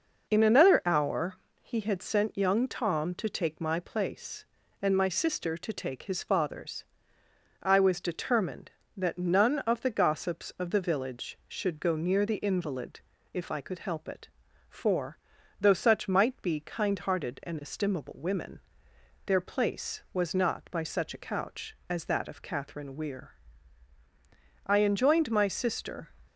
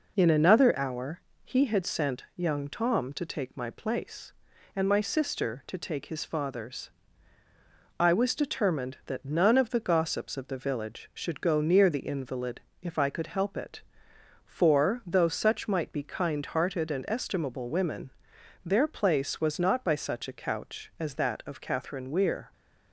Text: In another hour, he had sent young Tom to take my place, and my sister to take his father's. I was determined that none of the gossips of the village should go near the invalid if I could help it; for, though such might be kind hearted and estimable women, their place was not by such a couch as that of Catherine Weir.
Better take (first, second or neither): second